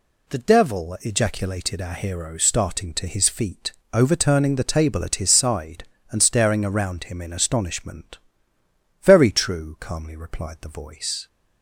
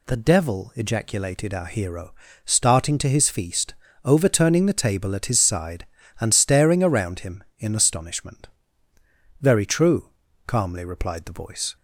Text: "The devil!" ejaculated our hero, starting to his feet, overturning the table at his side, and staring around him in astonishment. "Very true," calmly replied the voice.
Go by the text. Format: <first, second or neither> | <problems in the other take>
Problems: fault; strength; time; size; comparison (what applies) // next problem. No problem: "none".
first | says "feast" for "feet"; at 3.2 s